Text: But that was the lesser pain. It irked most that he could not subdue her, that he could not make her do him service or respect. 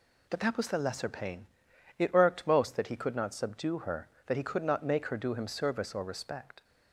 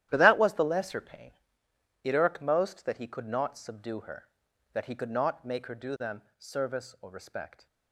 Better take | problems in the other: first | starts louder than the rest; strong; until 1.1 s; 12 dB // says "them" for "him"; at 5.9 s

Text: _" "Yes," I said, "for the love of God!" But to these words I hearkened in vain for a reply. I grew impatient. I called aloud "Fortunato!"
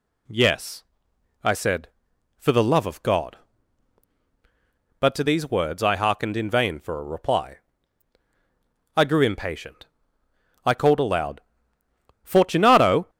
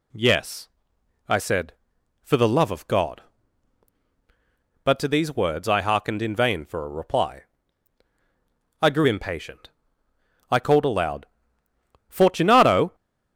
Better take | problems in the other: neither | pauses between "aloud" and "Fortunato"; noticeable; the same in both

